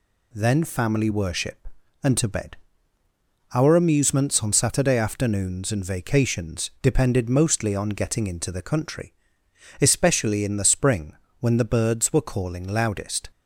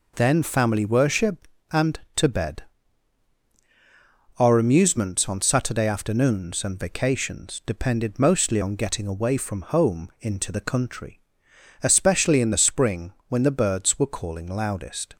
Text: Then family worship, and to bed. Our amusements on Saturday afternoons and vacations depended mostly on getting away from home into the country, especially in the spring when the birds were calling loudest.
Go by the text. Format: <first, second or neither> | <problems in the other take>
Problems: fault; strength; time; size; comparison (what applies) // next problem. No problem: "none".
second | skips "away from home"; at 8.2 s // pauses between "spring" and "when"; slight; at 11.1 s; 0.24 s long; slight in the second